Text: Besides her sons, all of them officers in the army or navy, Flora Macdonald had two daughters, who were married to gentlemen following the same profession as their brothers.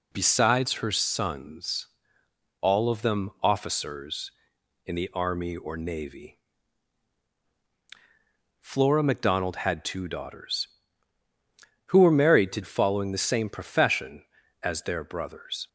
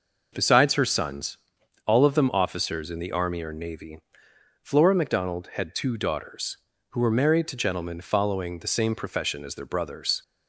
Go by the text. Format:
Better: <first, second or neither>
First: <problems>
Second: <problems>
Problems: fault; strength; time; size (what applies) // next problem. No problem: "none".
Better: second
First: skips "gentlemen"; at 12.6 s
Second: none